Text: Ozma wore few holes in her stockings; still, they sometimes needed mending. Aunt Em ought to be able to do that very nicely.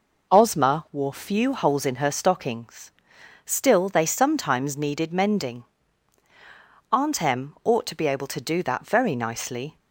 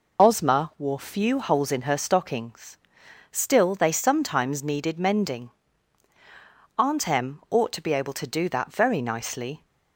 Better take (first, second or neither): first